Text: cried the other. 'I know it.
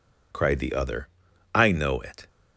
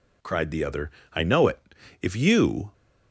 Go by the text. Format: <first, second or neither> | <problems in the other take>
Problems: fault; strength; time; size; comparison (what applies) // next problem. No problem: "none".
first | goes on to say "If you"; noticeable; from 2.0 s on; 0.70 s long